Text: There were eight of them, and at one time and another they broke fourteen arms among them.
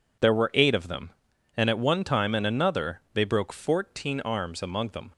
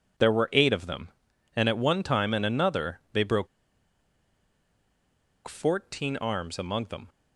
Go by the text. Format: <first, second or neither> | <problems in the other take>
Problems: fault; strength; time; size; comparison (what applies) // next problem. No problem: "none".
first | pauses between "broke" and "fourteen"; strong; at 3.4 s; 2.0 s long